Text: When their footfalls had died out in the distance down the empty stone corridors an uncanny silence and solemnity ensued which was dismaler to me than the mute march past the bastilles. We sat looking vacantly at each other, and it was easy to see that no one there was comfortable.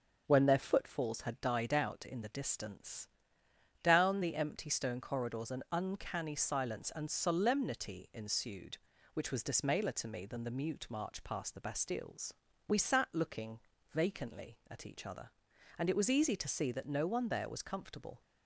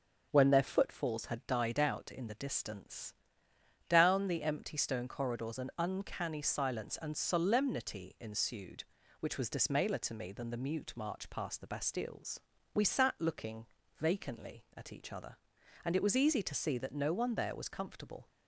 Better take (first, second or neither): neither